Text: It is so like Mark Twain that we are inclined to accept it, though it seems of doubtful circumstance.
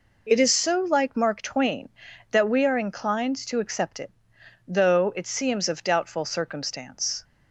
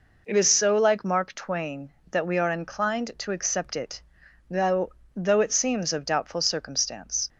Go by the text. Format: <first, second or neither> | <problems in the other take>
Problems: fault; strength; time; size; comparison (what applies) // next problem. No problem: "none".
first | says "though" twice; at 5.1 s